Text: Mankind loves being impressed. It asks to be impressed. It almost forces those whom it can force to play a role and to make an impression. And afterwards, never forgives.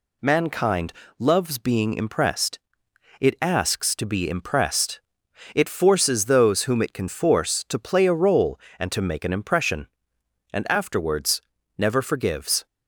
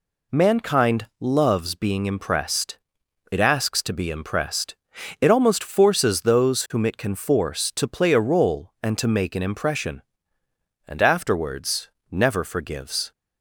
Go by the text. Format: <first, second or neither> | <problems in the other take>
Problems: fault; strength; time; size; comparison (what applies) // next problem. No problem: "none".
second | pauses between "Mankind" and "loves"; slight; at 0.9 s; 0.26 s long // skips "almost"; at 5.6 s